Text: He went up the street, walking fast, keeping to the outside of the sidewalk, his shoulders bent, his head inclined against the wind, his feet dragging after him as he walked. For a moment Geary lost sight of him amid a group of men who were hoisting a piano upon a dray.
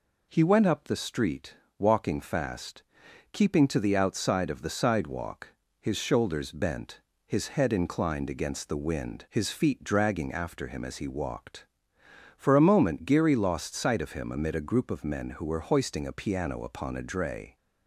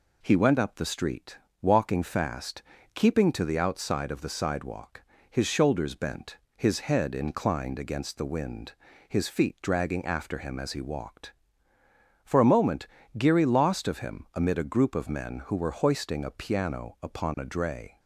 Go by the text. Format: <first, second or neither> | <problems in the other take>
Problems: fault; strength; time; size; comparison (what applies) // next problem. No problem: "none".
first | pauses between "moment" and "Geary"; slight; at 12.8 s; 0.30 s long // skips "sight"; at 13.8 s